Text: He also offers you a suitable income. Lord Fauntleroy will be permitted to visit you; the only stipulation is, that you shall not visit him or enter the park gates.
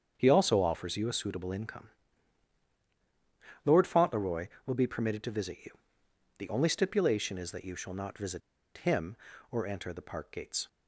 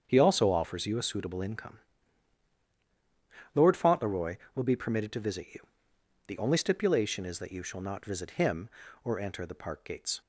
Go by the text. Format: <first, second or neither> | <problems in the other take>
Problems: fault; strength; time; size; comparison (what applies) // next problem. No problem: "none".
second | starts louder than the rest; strong; until 1.1 s; 7.5 dB; strong in the second // pauses between "visit" and "him"; at 8.4 s; 0.36 s long